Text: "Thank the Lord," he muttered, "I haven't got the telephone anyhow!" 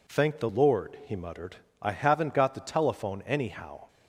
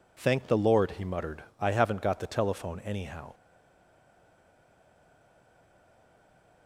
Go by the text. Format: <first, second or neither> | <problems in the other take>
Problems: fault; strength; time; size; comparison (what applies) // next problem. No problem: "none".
first | stays silent after the last word; strong; from 3.3 s on; 3.3 s long